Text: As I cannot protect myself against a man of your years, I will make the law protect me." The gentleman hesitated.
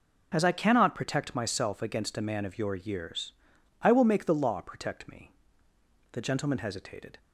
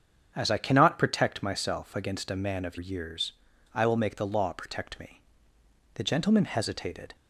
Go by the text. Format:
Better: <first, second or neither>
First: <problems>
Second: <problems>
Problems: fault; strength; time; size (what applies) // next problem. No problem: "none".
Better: first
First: none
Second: starts louder than the rest; strong; until 1.3 s; 7.5 dB // skips "your"; at 2.7 s